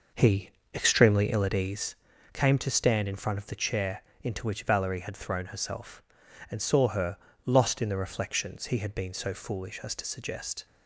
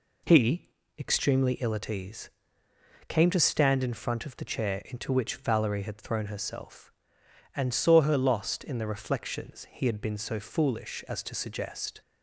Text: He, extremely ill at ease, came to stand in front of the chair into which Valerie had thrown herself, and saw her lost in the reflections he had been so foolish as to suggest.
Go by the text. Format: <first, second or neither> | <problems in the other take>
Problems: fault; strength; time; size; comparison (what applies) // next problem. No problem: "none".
second | starts louder than the rest; noticeable; until 1.9 s; 5.5 dB // pauses between "chair" and "into"; slight; at 4.0 s; 0.18 s long // pauses between "her" and "lost"; slight; at 7.1 s; 0.28 s long